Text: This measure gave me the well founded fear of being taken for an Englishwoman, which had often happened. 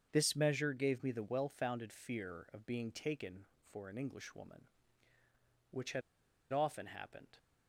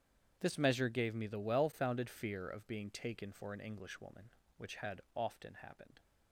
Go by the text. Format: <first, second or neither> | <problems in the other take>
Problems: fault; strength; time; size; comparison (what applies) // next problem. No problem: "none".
second | starts louder than the rest; strong; until 1.1 s; 7 dB; strong in the second // pauses between "had" and "often"; noticeable; at 6.0 s; 0.50 s long